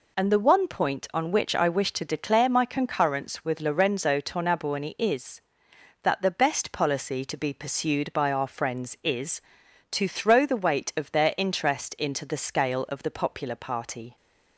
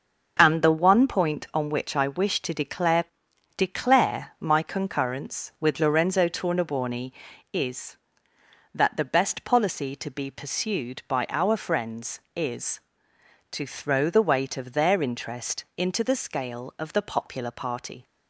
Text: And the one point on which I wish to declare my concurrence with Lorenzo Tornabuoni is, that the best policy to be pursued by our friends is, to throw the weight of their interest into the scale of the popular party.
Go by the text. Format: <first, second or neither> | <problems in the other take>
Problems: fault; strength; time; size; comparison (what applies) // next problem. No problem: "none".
first | starts louder than the rest; noticeable; until 1.4 s; 6 dB // says "declare" twice; at 3.5 s